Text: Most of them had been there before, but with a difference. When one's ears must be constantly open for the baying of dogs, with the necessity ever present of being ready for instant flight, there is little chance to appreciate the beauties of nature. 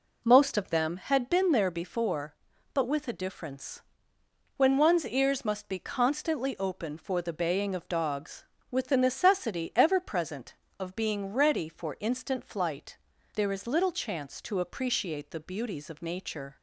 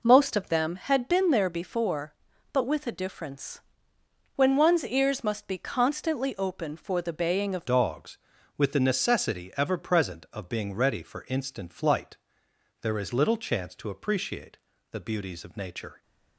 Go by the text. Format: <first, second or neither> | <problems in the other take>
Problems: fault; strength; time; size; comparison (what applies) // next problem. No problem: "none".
first | changes voice at "dogs"; from 7.6 s on; 8.4 s long // pauses between "appreciate" and "the"; slight; at 14.5 s; 0.34 s long